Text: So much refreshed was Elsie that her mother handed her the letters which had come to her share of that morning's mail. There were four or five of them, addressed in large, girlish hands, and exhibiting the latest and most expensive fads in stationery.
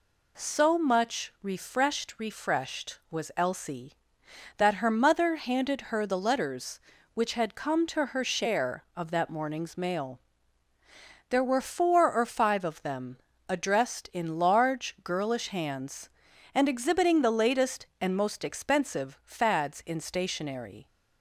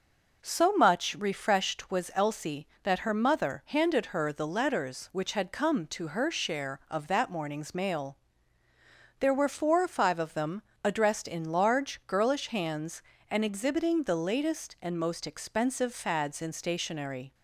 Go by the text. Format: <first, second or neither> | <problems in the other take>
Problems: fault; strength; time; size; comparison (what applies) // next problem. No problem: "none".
second | says "refreshed" twice; at 2.2 s